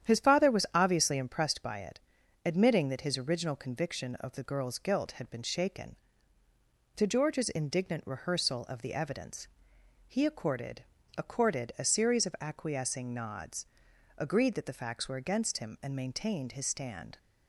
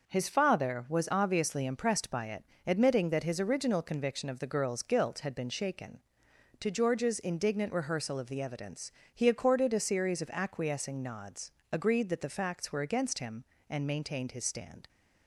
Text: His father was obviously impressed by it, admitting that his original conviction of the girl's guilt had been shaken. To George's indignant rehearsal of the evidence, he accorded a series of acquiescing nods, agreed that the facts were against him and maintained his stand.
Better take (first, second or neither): second